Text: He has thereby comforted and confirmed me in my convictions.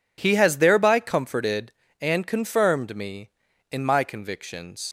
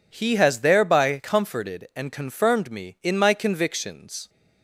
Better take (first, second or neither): second